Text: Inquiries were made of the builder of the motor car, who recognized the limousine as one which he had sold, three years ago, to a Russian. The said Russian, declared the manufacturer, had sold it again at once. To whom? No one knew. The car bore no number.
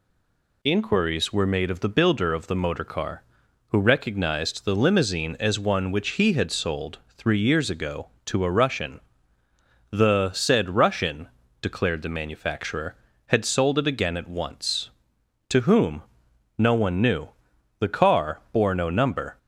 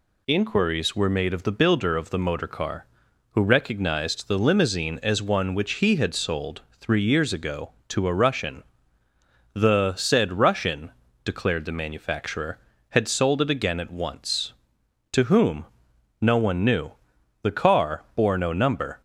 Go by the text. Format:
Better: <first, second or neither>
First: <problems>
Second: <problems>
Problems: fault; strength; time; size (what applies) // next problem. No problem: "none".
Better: second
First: stays silent before the first word; slight; until 0.6 s; 0.6 s long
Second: none